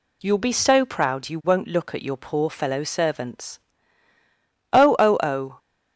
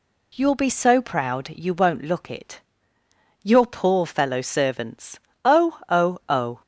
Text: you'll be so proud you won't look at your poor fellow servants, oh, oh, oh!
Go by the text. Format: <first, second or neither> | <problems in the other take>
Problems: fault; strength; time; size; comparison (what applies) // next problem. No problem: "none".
first | says "it" for "at"; at 2.2 s